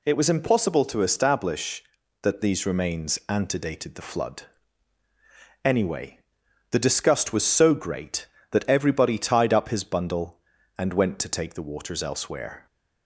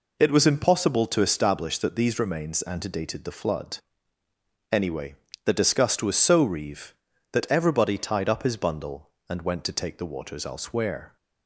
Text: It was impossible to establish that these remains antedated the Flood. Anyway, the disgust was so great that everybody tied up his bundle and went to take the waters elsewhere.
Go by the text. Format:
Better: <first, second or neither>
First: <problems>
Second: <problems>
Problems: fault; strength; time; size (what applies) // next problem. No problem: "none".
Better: first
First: none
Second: says "reeve" for "great"; at 6.4 s